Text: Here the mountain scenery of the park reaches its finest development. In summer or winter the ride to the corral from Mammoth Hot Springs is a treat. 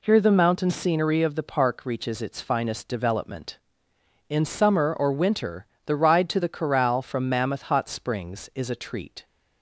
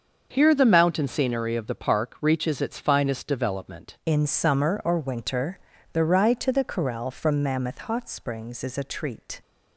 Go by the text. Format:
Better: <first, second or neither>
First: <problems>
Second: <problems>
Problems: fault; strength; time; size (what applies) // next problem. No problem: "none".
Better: first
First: pauses between "winter" and "the"; slight; at 5.6 s; 0.18 s long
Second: starts louder than the rest; until 1.3 s; 6.5 dB // changes voice at "In"; from 4.0 s on; 5.4 s long // pauses between "winter" and "the"; slight; at 5.5 s; 0.36 s long